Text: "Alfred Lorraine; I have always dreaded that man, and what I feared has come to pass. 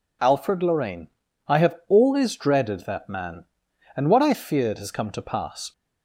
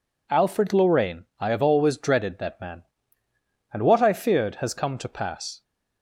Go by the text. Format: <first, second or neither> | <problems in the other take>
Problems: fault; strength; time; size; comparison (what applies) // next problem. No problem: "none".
neither | none